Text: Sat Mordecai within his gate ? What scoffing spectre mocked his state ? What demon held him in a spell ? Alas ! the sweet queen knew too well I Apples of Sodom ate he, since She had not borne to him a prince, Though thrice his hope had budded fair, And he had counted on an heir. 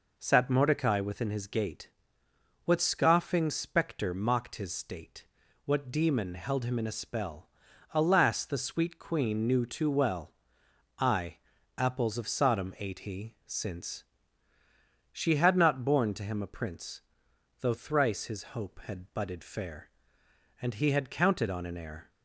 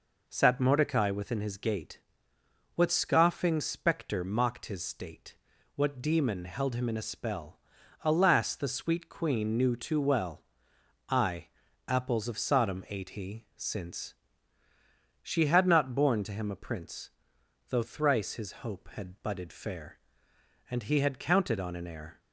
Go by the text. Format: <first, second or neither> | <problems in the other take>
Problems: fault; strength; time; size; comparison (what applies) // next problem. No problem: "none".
neither | pauses between "well" and "I"; noticeable; the same in both // pauses between "I" and "Apples"; the same in both // pauses between "since" and "She"; the same in both